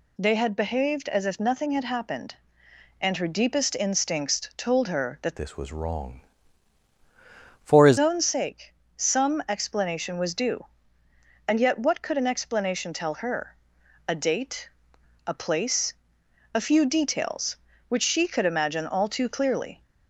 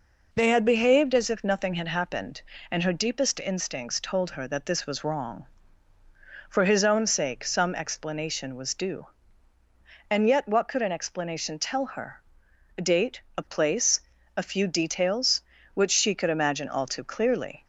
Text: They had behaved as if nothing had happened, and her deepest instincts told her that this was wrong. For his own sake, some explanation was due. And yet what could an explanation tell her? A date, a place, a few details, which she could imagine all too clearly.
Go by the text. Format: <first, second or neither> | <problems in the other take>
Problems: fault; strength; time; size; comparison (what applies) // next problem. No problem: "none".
second | changes voice from "this" to "his"; from 5.3 to 7.9 s; 2.6 s long